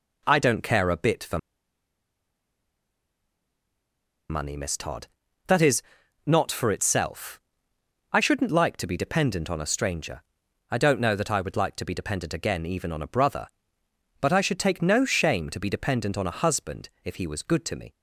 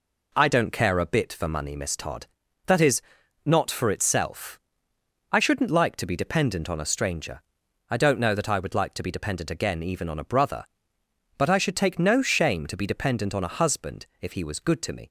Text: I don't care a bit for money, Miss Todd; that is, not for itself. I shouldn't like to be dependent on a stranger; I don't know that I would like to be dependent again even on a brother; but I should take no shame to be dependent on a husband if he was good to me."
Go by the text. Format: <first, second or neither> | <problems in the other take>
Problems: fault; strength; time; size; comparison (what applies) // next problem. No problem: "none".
second | pauses between "for" and "money"; strong; at 1.3 s; 2.9 s long // pauses between "husband" and "if"; slight; at 16.8 s; 0.16 s long; slight in the second